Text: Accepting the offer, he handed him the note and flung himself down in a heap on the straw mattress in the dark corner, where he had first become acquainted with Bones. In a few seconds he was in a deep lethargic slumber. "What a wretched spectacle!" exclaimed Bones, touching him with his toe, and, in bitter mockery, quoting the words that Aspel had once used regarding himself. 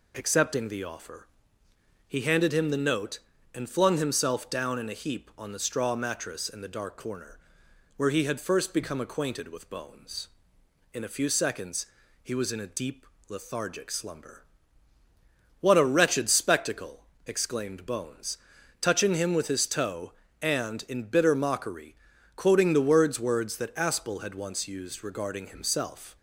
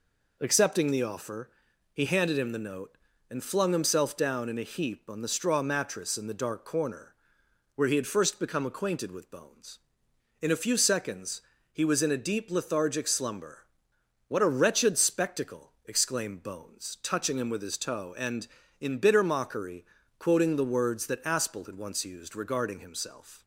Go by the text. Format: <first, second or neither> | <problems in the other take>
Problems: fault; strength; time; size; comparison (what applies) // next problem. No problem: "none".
second | pauses between "seconds" and "he"; at 11.8 s; 0.38 s long; slight in the second // pauses between "deep" and "lethargic"; slight; at 13.0 s; 0.22 s long // says "words" twice; at 23.1 s